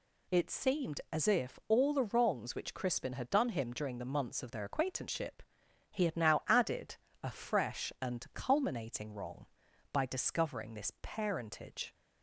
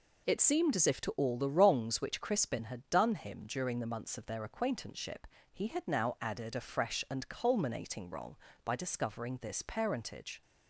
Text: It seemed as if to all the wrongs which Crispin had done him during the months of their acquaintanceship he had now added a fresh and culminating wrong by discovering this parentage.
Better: second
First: skips "to"; at 1.6 s // pauses between "acquaintanceship" and "he"; noticeable; at 5.4 s; 0.48 s long // pauses between "added" and "a"; slight; at 6.9 s; 0.26 s long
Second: pauses between "acquaintanceship" and "he"; slight; at 5.2 s; 0.26 s long

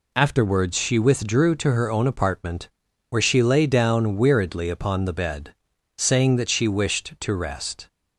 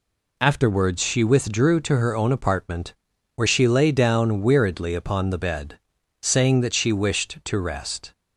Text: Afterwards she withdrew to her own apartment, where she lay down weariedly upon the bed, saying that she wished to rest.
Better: neither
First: none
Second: none

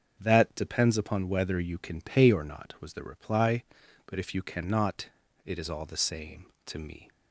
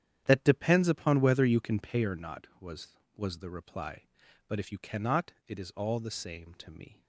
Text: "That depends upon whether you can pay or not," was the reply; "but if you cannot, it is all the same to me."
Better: first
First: starts louder than the rest; until 1.2 s; 6.5 dB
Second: starts louder than the rest; strong; until 1.2 s; 9.5 dB // says "was" twice; at 3.1 s

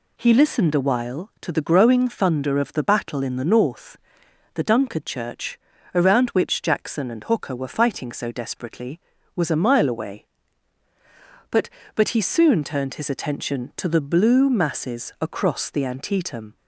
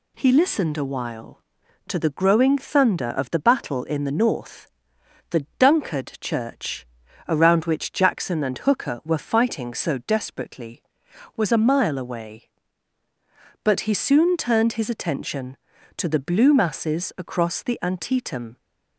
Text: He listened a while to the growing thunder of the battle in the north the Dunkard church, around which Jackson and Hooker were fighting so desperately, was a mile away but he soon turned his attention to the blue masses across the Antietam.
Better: second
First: pauses between "north" and "the"; noticeable; at 3.9 s; 0.56 s long // says "but" twice; at 11.9 s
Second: pauses between "north" and "the"; noticeable; at 4.6 s; 0.64 s long

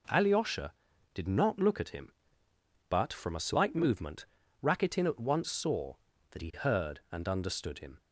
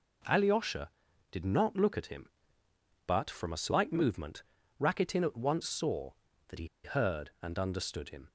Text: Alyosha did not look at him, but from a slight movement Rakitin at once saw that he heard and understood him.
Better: first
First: pauses between "movement" and "Rakitin"; slight; at 4.2 s; 0.36 s long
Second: pauses between "movement" and "Rakitin"; slight; at 4.4 s; 0.36 s long // pauses between "he" and "heard"; slight; at 6.6 s; 0.17 s long

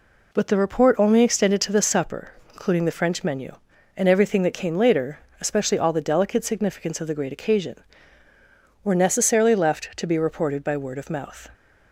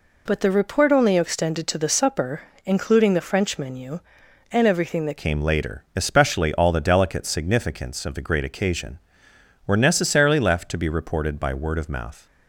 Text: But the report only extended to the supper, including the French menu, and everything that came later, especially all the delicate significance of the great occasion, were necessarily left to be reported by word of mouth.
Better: first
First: none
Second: changes voice at "came"; from 5.1 s on; 7.1 s long

